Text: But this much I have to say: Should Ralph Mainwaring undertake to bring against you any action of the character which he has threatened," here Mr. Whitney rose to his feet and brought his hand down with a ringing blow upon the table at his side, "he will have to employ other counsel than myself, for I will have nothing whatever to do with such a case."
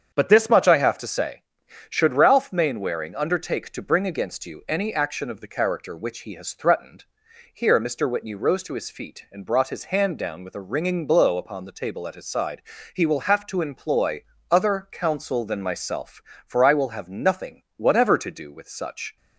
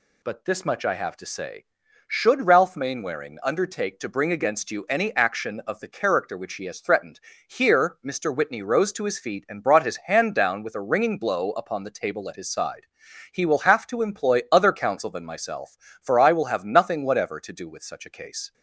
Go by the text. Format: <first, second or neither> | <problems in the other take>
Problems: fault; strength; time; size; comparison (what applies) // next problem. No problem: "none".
second | starts louder than the rest; strong; until 1.1 s; 7.5 dB // pauses between "employ" and "other"; slight; at 14.2 s; 0.28 s long // pauses between "nothing" and "whatever"; slight; at 17.6 s; 0.16 s long // stops before "a case"; at 19.1 s